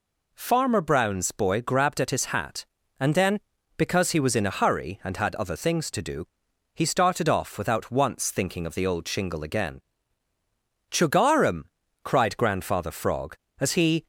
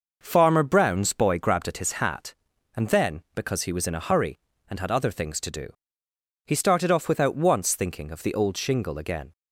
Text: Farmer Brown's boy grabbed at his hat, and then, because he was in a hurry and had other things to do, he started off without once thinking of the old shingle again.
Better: second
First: goes on to say "Chugarum cried Grandfather Frog as he"; strong; from 10.8 s on; 3.1 s long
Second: none

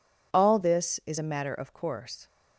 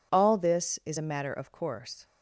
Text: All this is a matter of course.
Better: neither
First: none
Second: none

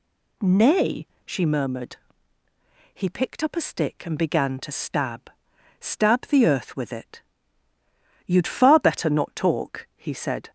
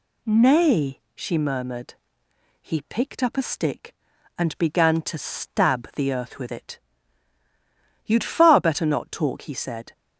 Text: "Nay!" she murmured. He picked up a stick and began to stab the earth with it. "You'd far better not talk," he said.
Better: second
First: says "stab" twice; at 5.7 s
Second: none

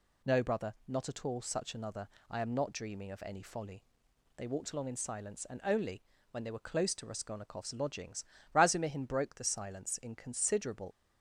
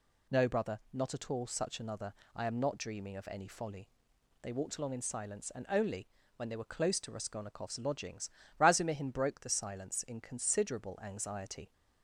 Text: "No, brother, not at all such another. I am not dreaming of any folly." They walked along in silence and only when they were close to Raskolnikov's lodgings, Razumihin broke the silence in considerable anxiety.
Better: second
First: pauses between "only" and "when"; slight; at 6.0 s; 0.30 s long // stops before "anxiety"; at 10.9 s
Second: pauses between "only" and "when"; slight; at 6.0 s; 0.30 s long

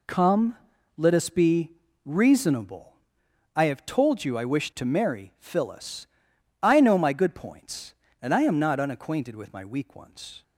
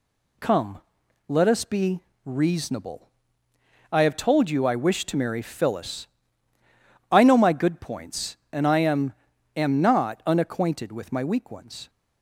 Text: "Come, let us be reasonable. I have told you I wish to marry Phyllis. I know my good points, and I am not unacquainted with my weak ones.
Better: first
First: pauses between "be" and "reasonable"; slight; at 1.7 s; 0.32 s long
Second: pauses between "be" and "reasonable"; slight; at 2.0 s; 0.22 s long // says "am" twice; at 9.5 s

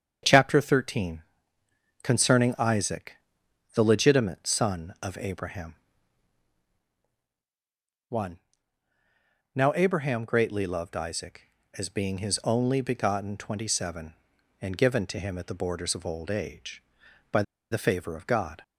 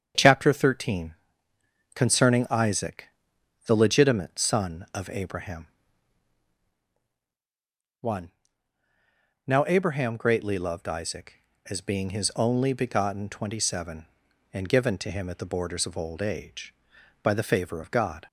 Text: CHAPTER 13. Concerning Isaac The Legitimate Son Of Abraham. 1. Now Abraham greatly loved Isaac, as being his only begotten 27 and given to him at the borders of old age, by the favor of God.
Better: second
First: starts louder than the rest; strong; until 2.0 s; 7.5 dB // pauses between "Isaac" and "The"; noticeable; at 3.1 s; 0.58 s long // pauses between "by" and "the"; slight; at 17.4 s; 0.29 s long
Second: starts louder than the rest; strong; until 1.9 s; 7.5 dB // pauses between "Isaac" and "The"; noticeable; at 3.0 s; 0.58 s long

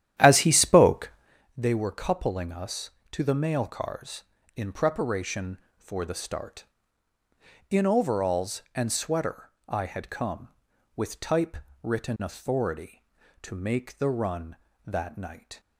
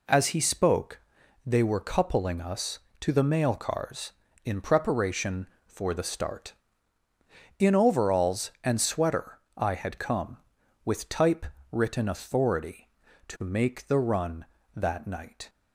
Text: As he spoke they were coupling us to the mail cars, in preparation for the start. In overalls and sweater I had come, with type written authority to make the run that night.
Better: second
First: starts louder than the rest; strong; until 1.3 s; 11.5 dB // pauses between "spoke" and "they"; at 1.1 s; 0.44 s long // pauses between "sweater" and "I"; slight; at 9.4 s; 0.18 s long // pauses between "type" and "written"; slight; at 11.5 s; 0.26 s long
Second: pauses between "spoke" and "they"; at 0.9 s; 0.44 s long // pauses between "sweater" and "I"; slight; at 9.3 s; 0.18 s long // pauses between "type" and "written"; slight; at 11.4 s; 0.26 s long

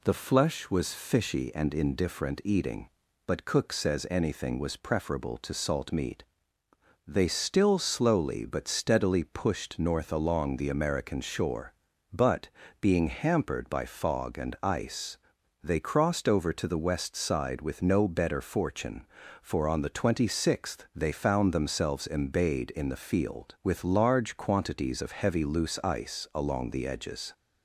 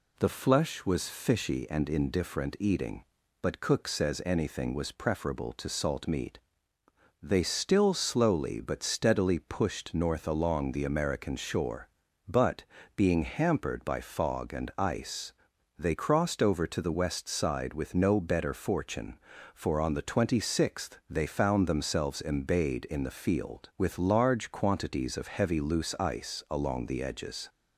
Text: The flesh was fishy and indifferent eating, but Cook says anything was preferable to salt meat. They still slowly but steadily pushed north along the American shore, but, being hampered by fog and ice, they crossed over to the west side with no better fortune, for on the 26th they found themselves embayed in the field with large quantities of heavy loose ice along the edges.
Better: neither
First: none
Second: none

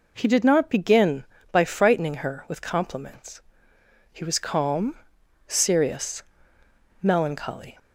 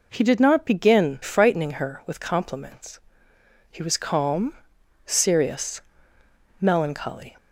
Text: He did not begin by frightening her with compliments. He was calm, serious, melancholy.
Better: first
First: none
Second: skips "by"; at 1.2 s

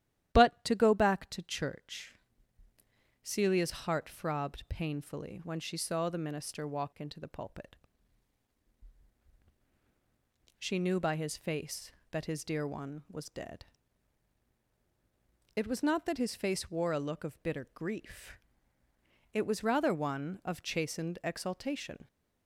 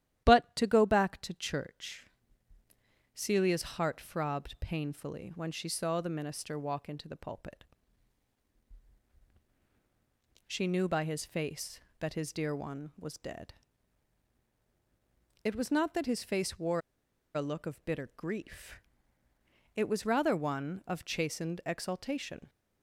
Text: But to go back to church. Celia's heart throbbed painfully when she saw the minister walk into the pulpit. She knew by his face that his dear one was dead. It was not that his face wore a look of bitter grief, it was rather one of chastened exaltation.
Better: first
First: starts louder than the rest; strong; until 1.3 s; 12 dB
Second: starts louder than the rest; strong; until 1.2 s; 12 dB // pauses between "wore" and "a"; noticeable; at 16.7 s; 0.55 s long

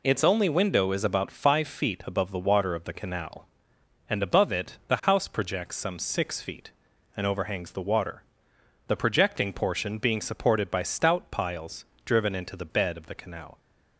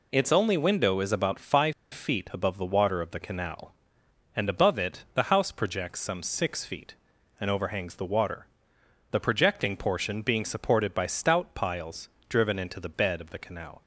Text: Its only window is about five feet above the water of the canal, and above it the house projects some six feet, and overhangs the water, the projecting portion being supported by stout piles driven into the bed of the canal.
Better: first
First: pauses between "piles" and "driven"; slight; at 11.8 s; 0.20 s long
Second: pauses between "five" and "feet"; slight; at 1.7 s; 0.20 s long // pauses between "piles" and "driven"; slight; at 12.0 s; 0.20 s long

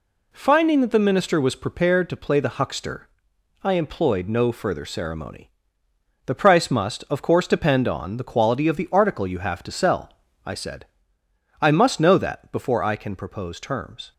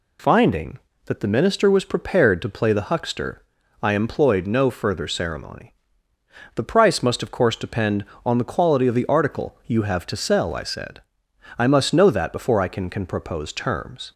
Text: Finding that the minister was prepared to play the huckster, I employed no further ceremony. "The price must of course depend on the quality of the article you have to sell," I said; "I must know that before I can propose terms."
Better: first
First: none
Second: says "can" twice; at 12.9 s

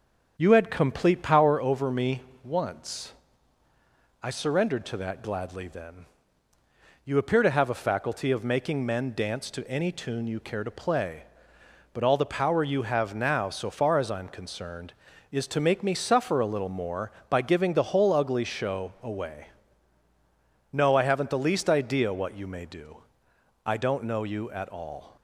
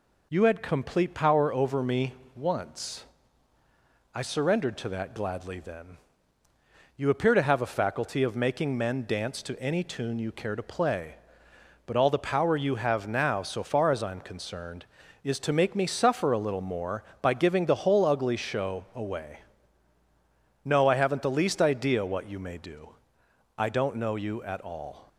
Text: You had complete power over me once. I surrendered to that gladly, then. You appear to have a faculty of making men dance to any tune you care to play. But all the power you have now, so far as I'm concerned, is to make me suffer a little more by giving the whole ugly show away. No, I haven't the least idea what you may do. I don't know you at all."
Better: second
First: starts louder than the rest; strong; until 1.7 s; 7.5 dB // pauses between "me" and "once"; slight; at 2.2 s; 0.22 s long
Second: pauses between "me" and "once"; slight; at 2.1 s; 0.22 s long

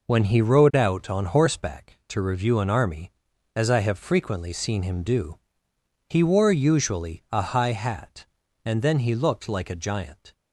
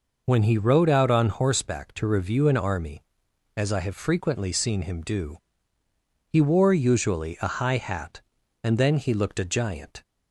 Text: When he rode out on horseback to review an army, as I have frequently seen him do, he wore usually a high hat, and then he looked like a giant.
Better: first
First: none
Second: skips "like"; at 9.3 s

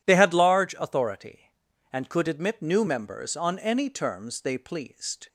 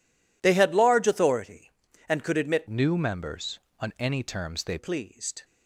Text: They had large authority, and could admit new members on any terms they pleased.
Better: first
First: none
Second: changes voice from "new" to "they"; from 2.6 to 4.7 s; 2.1 s long

